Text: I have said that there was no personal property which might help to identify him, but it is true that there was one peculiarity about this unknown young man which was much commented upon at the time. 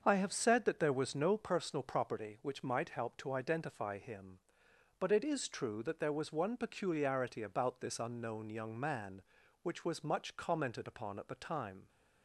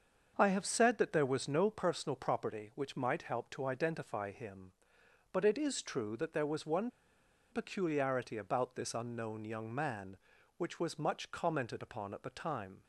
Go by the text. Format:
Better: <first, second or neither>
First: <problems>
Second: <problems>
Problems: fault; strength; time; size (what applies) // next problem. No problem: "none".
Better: first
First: starts louder than the rest; until 1.0 s; 7 dB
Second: starts louder than the rest; until 1.3 s; 7 dB // pauses between "one" and "peculiarity"; noticeable; at 6.8 s; 0.62 s long